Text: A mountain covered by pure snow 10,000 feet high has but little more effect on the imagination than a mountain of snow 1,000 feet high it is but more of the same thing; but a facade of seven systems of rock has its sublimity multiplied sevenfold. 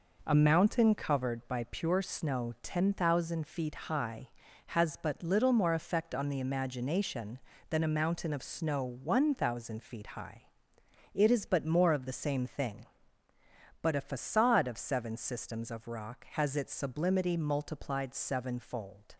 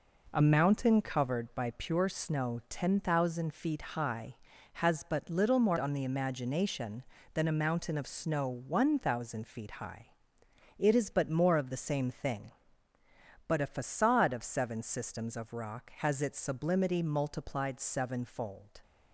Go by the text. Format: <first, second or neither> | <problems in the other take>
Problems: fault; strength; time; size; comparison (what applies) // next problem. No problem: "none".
first | skips "effect"; at 5.7 s // pauses between "high" and "it"; noticeable; at 10.0 s; 0.72 s long; noticeable in the first